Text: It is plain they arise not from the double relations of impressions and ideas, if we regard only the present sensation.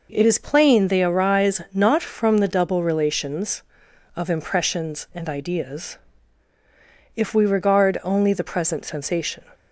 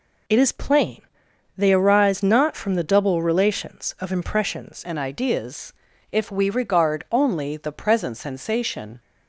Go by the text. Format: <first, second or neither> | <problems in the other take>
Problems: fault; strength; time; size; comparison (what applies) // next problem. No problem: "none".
first | pauses between "plain" and "they"; noticeable; at 1.0 s; 0.54 s long // changes voice at "and"; from 4.8 s on; 4.1 s long